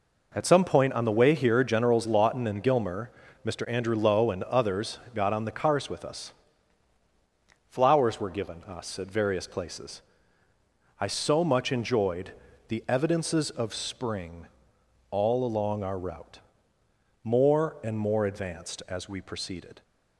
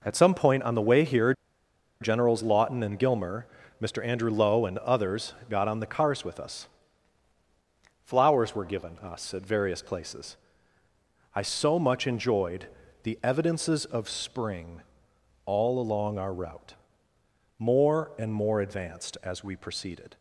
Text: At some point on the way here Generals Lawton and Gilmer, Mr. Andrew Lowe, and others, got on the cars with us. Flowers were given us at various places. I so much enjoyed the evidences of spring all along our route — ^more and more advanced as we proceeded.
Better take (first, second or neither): first